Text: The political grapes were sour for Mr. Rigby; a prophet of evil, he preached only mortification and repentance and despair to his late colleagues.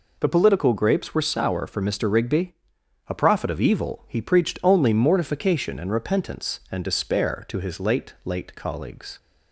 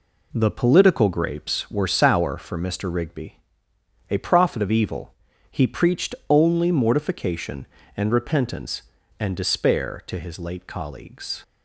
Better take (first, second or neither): second